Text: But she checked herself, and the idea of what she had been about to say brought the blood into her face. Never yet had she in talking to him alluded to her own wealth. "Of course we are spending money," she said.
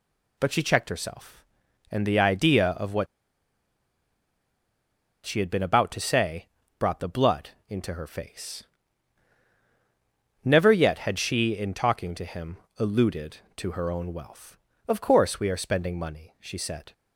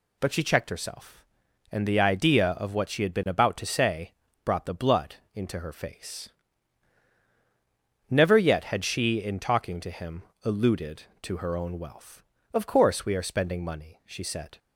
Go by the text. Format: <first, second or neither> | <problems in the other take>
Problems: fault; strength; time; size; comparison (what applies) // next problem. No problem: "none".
second | pauses between "what" and "she"; strong; at 3.0 s; 2.2 s long // pauses between "say" and "brought"; slight; at 6.4 s; 0.32 s long; slight in the second // pauses between "blood" and "into"; slight; at 7.5 s; 0.18 s long; slight in the second // pauses between "him" and "alluded"; slight; at 12.5 s; 0.22 s long; slight in the second